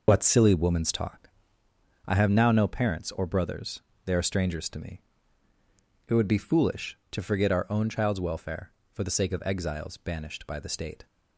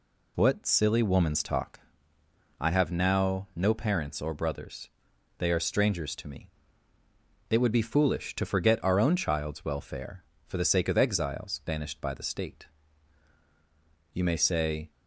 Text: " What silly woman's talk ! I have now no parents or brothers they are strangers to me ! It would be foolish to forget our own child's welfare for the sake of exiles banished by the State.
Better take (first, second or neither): first